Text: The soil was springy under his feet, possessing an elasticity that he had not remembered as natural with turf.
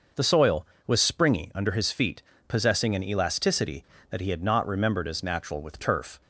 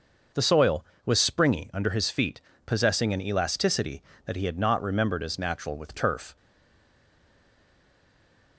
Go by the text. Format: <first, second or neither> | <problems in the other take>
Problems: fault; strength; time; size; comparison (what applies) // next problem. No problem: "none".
first | stays silent after the last word; from 6.3 s on; 2.2 s long